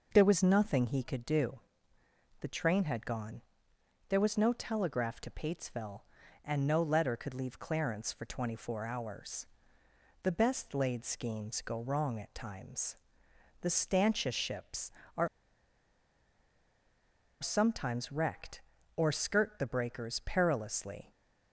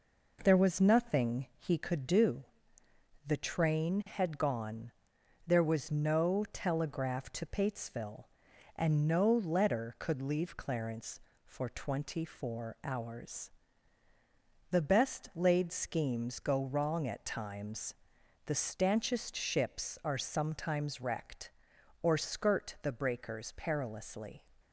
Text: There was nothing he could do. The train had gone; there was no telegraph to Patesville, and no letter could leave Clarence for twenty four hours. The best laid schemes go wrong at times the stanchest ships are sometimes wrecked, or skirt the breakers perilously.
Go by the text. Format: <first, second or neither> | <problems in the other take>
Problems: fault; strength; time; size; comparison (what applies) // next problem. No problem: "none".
second | pauses between "times" and "the"; noticeable; at 12.9 s; 0.66 s long; noticeable in the second // pauses between "are" and "sometimes"; strong; at 15.2 s; 2.1 s long